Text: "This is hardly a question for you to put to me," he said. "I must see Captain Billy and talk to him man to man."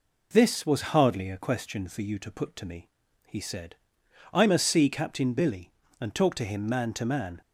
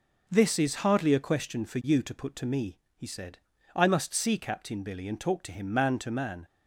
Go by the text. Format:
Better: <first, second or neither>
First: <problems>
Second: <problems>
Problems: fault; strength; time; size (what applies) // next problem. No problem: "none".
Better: second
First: says "was" for "is"; at 0.6 s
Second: none